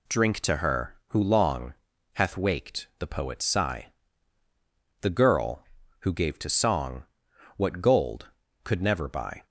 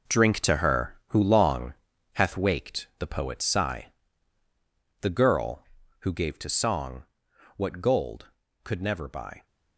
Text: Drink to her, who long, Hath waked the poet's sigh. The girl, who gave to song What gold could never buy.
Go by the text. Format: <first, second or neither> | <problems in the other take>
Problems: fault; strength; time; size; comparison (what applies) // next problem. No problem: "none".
first | gets quieter; strong; throughout; 10.5 dB // pauses between "song" and "What"; noticeable; at 7.0 s; 0.54 s long; noticeable in the first